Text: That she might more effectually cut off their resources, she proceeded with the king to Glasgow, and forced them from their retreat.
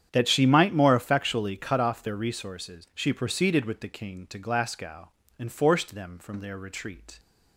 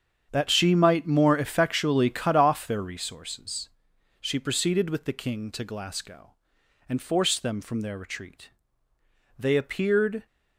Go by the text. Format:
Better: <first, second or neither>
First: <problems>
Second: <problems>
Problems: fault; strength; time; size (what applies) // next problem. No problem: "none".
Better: first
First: starts louder than the rest; strong; until 1.1 s; 9 dB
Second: starts louder than the rest; strong; until 1.3 s; 8 dB // goes on to say "They appeared"; noticeable; from 9.3 s on; 0.88 s long